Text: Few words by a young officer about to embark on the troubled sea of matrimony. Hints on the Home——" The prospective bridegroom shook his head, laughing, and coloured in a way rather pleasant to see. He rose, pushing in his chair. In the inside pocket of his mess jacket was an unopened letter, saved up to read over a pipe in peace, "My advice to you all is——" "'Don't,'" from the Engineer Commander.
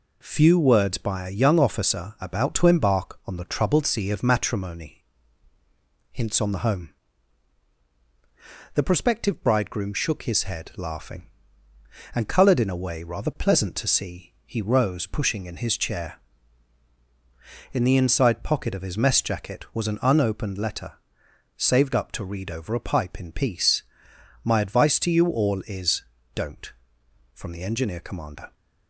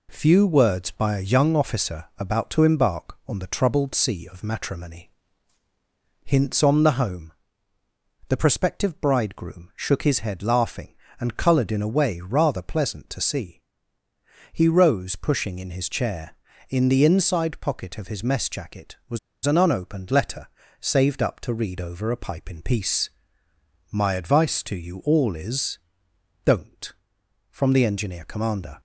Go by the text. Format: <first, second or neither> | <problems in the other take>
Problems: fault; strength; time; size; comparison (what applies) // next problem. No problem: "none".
first | pauses between "was" and "an"; slight; at 19.1 s; 0.27 s long